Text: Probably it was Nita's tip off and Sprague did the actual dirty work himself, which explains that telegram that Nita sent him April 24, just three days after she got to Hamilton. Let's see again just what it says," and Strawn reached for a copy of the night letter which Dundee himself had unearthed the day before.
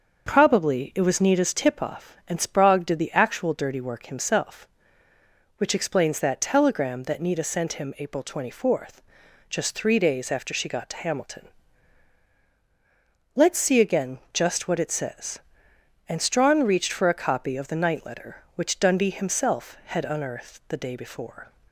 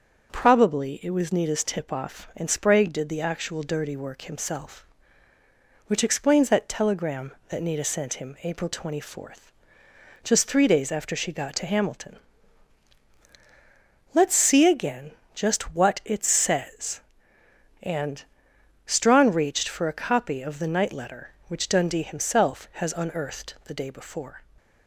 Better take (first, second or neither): first